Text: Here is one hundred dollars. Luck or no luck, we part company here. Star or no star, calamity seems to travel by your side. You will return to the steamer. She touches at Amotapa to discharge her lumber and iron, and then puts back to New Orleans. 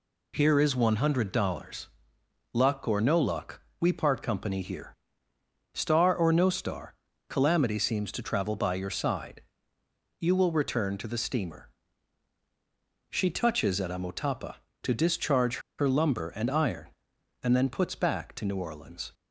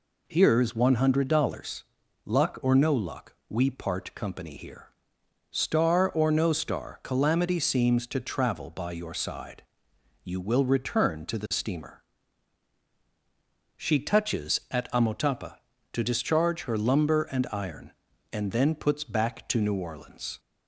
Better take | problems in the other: second | pauses between "discharge" and "her"; slight; at 15.5 s; 0.19 s long

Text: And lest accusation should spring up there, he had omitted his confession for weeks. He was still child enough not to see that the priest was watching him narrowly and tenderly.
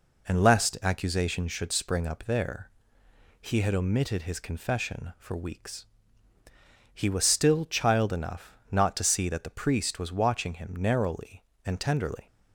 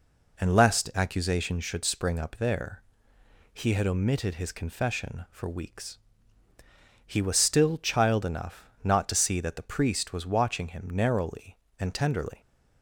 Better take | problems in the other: neither | pauses between "enough" and "not"; slight; the same in both

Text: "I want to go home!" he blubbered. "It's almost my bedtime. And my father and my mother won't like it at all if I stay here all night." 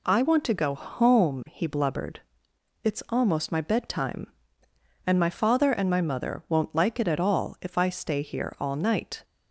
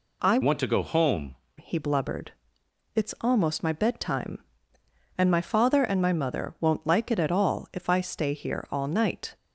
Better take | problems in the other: first | changes voice from "want" to "home"; from 0.4 to 1.3 s; 0.9 s long

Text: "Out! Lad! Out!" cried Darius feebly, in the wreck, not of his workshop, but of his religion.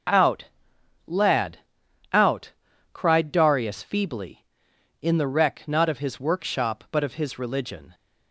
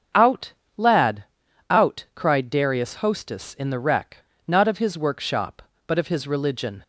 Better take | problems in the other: first | starts louder than the rest; strong; until 1.8 s; 7.5 dB; also in the first // says "hostess" for "feebly"; at 2.9 s

